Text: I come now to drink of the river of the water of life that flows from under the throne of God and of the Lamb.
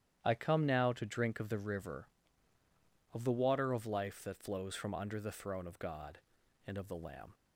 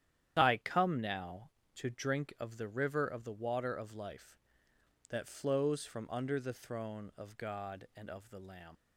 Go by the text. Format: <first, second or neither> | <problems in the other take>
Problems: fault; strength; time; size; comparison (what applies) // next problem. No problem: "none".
first | starts louder than the rest; strong; until 1.3 s; 10.5 dB; strong in the first // leaves "Lamb" unfinished; at 8.7 s; 85 ms